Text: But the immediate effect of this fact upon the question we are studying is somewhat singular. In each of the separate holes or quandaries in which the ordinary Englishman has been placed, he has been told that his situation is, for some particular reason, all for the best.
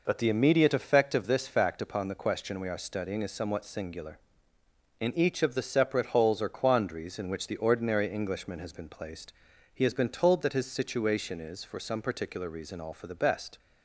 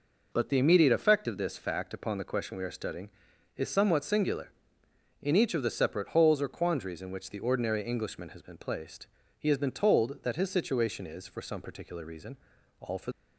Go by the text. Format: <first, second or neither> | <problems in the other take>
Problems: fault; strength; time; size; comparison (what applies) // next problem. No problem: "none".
first | stops before "the best"; at 13.1 s